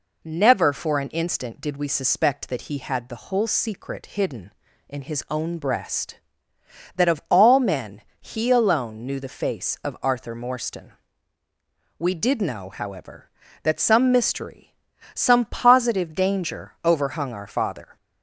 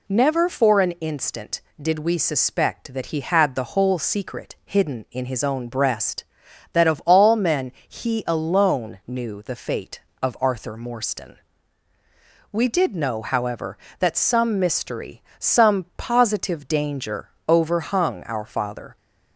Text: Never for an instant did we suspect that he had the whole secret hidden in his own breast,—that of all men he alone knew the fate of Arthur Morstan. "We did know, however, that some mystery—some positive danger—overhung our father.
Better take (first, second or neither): second